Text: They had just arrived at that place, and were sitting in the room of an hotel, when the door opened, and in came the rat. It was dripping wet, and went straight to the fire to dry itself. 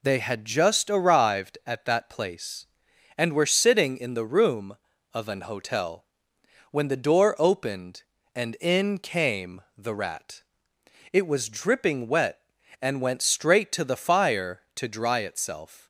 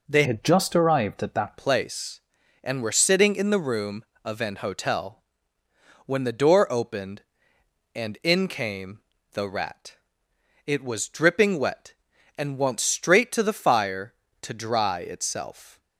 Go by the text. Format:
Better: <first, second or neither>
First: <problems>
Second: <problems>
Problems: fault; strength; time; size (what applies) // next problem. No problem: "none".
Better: first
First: pauses between "came" and "the"; slight; at 9.6 s; 0.16 s long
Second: changes voice from "had" to "that"; from 0.2 to 1.5 s; 1.3 s long // pauses between "came" and "the"; slight; at 8.9 s; 0.32 s long